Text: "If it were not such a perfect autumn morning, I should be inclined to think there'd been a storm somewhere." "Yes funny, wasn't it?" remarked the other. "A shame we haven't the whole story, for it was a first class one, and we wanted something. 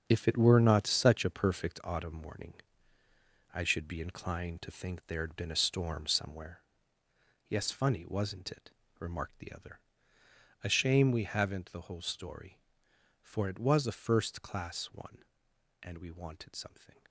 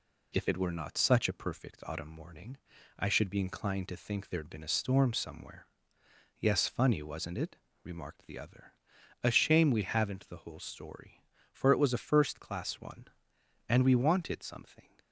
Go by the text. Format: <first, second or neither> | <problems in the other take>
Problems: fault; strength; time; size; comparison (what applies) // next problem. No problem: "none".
second | gets quieter; strong; throughout; 10 dB